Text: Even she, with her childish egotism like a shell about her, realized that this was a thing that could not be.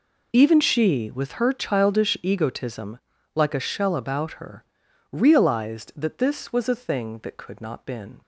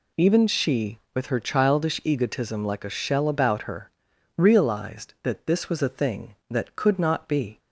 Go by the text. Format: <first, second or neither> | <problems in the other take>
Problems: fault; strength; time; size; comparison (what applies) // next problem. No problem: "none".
second | pauses between "egotism" and "like"; slight; at 2.9 s; 0.36 s long // says "been" for "be"; at 7.8 s